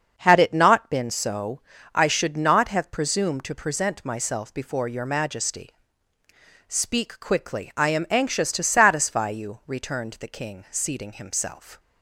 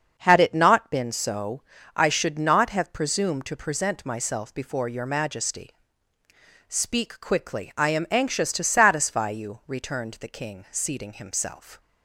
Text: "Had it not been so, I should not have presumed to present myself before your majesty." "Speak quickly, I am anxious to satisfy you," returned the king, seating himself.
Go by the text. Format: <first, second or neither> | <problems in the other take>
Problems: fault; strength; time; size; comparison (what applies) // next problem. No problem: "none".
neither | starts louder than the rest; the same in both